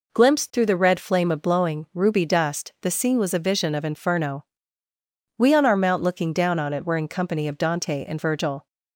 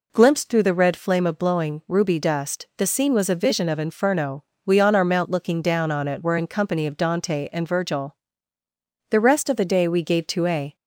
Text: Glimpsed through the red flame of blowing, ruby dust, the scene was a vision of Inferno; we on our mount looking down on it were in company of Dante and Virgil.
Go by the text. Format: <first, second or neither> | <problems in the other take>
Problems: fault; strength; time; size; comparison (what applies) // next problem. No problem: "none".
first | goes on to say "The rest of the day we gave to a"; from 9.1 s on; 1.6 s long